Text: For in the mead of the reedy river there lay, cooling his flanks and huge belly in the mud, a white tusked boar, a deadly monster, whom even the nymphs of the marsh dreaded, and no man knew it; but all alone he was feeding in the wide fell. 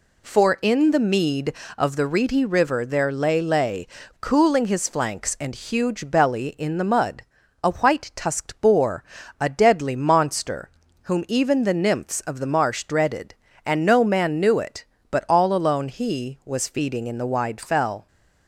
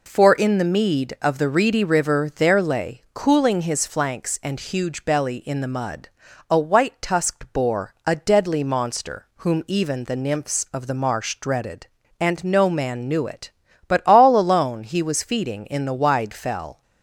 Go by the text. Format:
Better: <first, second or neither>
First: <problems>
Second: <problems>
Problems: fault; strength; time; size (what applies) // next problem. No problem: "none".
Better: second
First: says "lay" twice; at 3.4 s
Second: none